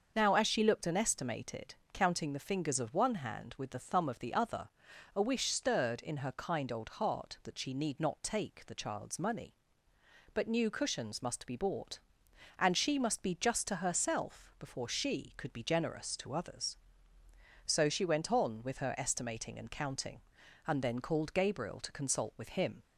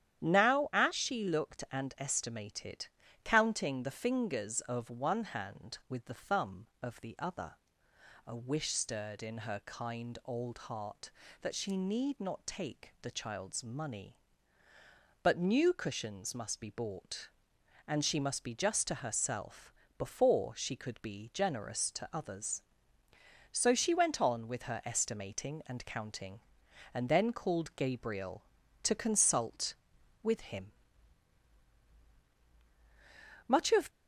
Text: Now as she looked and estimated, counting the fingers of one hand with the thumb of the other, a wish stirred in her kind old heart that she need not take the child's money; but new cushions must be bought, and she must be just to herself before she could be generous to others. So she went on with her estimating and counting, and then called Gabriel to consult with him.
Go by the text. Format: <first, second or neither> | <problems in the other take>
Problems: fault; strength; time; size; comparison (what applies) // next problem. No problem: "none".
first | starts louder than the rest; strong; until 1.2 s; 10 dB; also in the first // pauses between "herself" and "before"; slight; at 19.7 s; 0.28 s long // goes on to say "Much of"; slight; from 33.4 s on; 0.42 s long